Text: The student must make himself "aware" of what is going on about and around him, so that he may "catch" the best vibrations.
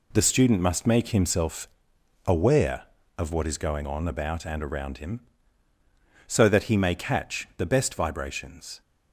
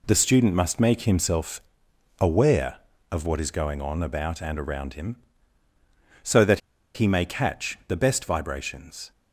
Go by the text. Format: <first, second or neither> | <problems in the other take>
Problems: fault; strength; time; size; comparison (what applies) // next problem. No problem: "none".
first | pauses between "himself" and "aware"; noticeable; at 1.6 s; 0.56 s long; noticeable in the first // pauses between "that" and "he"; slight; at 6.5 s; 0.35 s long